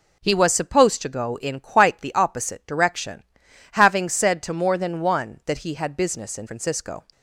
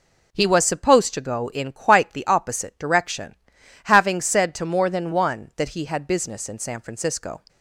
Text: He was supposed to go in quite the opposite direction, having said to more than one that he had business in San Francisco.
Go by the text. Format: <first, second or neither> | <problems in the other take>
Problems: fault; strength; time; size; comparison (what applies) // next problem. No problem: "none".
second | skips "San"; at 6.4 s